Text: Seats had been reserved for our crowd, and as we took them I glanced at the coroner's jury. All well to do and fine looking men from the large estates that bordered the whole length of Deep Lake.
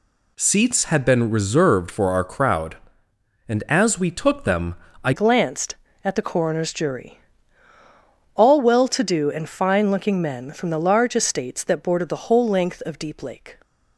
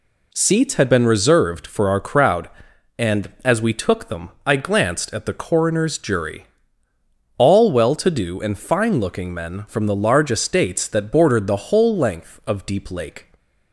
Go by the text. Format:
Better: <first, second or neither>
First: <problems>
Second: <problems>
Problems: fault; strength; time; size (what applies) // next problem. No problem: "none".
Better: second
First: pauses between "them" and "I"; slight; at 4.7 s; 0.30 s long // changes voice at "glanced"; from 5.1 s on; 8.4 s long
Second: pauses between "them" and "I"; slight; at 4.3 s; 0.16 s long